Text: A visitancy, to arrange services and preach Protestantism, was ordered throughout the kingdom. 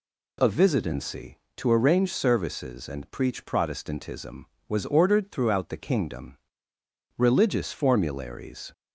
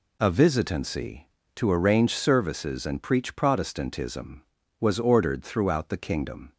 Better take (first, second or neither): second